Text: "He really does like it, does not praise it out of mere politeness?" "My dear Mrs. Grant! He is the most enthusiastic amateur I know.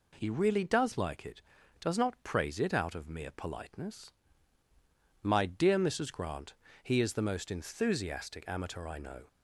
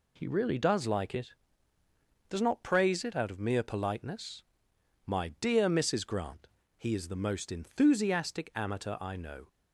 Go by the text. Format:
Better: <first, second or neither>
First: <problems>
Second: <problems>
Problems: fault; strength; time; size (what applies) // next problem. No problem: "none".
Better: neither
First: none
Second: none